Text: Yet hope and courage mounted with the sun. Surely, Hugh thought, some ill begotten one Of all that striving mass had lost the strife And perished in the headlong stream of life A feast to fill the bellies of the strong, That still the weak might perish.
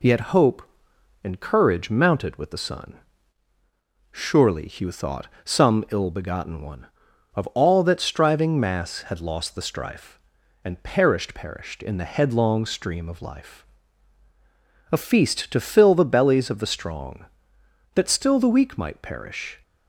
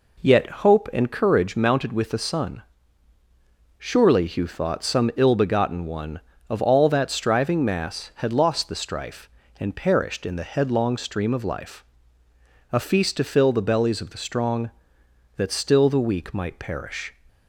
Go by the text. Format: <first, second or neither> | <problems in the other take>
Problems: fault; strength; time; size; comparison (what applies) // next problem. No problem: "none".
second | says "perished" twice; at 11.3 s // pauses between "life" and "A"; strong; at 13.6 s; 1.2 s long; noticeable in the second